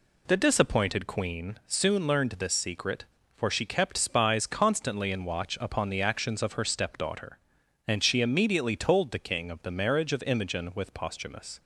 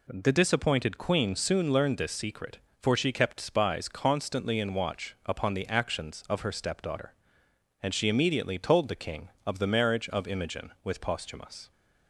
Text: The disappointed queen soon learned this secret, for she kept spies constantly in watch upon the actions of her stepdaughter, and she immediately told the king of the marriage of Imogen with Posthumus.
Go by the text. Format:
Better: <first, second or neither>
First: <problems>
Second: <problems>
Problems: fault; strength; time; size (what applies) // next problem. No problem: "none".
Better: neither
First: none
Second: none